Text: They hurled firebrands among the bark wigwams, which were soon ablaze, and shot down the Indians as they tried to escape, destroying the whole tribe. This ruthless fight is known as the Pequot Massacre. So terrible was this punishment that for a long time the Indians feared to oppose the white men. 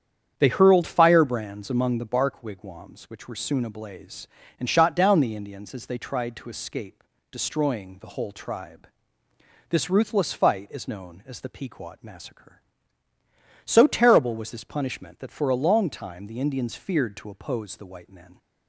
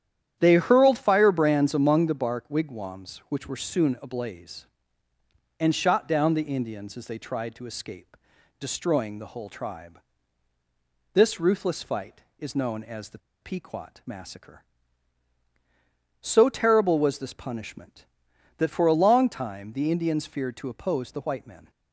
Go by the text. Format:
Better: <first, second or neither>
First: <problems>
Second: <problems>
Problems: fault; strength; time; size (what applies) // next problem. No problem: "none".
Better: first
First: starts louder than the rest; strong; until 1.4 s; 8.5 dB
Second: starts louder than the rest; strong; until 1.3 s; 10 dB // pauses between "the" and "Pequot"; slight; at 13.1 s; 0.22 s long